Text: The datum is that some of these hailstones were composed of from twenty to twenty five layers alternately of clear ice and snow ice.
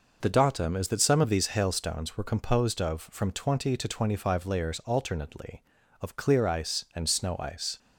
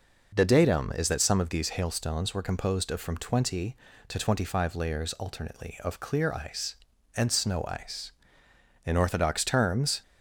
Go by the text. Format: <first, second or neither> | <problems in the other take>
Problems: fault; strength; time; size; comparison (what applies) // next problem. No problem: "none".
first | goes on to say "In orthodox terms"; noticeable; from 8.8 s on; 1.1 s long